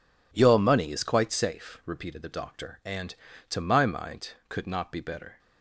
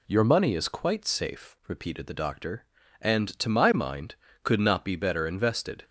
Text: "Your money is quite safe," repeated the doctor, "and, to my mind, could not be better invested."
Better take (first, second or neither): second